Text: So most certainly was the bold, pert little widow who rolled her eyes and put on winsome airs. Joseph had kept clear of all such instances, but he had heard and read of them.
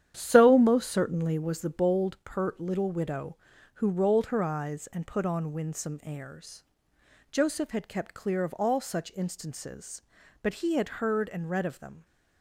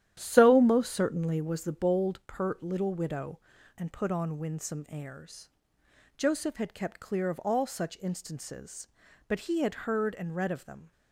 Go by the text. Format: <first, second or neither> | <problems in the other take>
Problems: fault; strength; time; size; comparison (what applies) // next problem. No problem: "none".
first | starts louder than the rest; strong; until 1.1 s; 11.5 dB; strong in the first // skips "who rolled her eyes"; at 3.5 s